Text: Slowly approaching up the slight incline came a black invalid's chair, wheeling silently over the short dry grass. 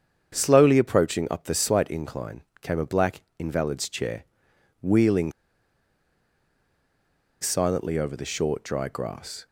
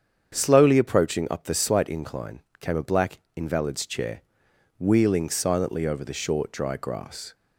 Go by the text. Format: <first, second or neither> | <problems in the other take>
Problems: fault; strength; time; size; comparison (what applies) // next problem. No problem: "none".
second | starts louder than the rest; strong; until 1.3 s; 7.5 dB; strong in the second // pauses between "incline" and "came"; slight; at 2.4 s; 0.20 s long; slight in the second // pauses between "black" and "invalid's"; slight; at 3.2 s; 0.16 s long; slight in the second // pauses between "wheeling" and "silently"; strong; at 5.3 s; 2.0 s long